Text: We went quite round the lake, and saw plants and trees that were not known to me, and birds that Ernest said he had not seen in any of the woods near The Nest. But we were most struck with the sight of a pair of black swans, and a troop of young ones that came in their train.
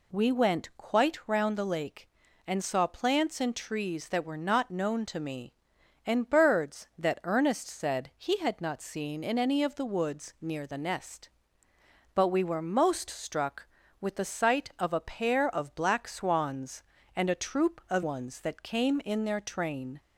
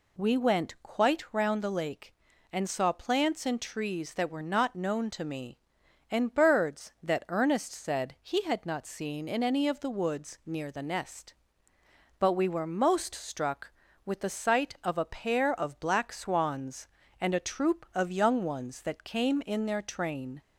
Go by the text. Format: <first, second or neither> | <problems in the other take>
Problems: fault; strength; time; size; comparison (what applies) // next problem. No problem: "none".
second | skips "young"; at 18.0 s